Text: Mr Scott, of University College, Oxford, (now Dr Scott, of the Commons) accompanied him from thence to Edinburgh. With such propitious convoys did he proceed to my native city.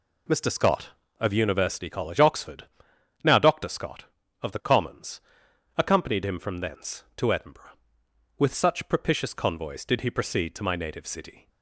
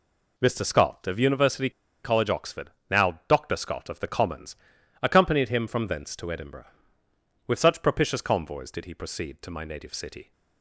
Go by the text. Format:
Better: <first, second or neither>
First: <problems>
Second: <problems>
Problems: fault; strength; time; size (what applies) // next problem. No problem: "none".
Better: first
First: none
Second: pauses between "University" and "College"; slight; at 1.7 s; 0.33 s long